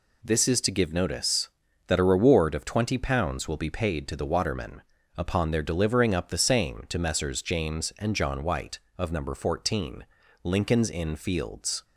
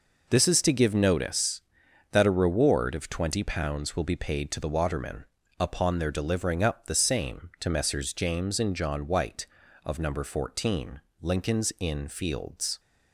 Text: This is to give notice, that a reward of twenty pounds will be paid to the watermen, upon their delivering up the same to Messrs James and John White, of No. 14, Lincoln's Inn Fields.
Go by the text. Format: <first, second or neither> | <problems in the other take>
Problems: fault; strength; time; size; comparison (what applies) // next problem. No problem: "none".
neither | none